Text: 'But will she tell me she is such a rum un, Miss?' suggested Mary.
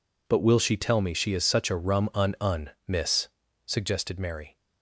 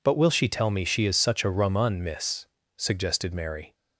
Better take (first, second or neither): second